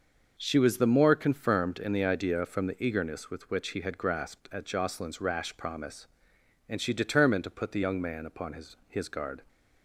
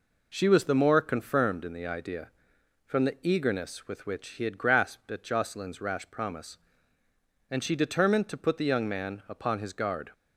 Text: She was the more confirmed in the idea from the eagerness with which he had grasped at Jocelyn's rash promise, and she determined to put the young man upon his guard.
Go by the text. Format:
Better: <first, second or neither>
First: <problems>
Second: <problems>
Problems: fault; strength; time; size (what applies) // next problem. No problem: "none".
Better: second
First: says "his" twice; at 8.8 s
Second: none